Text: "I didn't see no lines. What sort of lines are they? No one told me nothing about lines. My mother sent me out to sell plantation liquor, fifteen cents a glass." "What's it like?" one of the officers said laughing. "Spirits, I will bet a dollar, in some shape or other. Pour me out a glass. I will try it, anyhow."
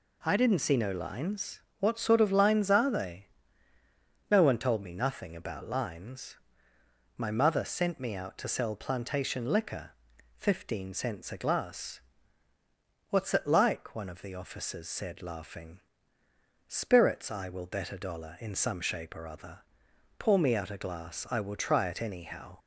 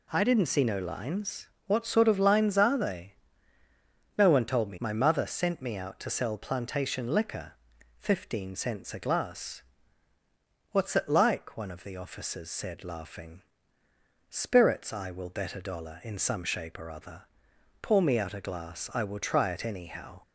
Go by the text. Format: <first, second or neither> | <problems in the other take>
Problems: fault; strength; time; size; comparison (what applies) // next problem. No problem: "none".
first | skips "nothing about lines"; at 4.7 s